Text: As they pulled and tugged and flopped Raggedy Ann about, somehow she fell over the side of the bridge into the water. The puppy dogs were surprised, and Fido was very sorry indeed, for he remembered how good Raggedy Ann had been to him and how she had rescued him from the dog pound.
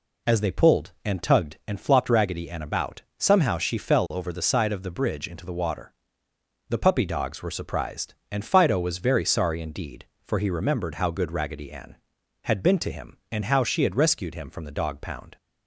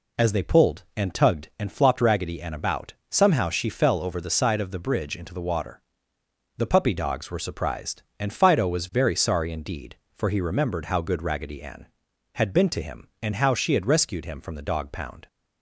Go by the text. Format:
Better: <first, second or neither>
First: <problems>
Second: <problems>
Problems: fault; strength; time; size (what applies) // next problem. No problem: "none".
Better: neither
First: none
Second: none